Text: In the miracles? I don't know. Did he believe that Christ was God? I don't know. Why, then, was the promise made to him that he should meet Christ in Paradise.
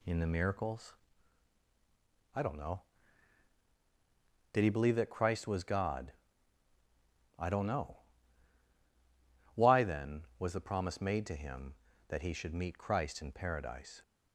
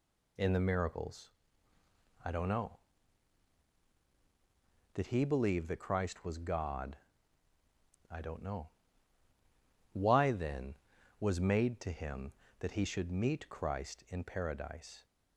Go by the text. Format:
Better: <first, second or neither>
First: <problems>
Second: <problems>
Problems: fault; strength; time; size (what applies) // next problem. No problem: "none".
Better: first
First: none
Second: skips "the promise"; at 11.3 s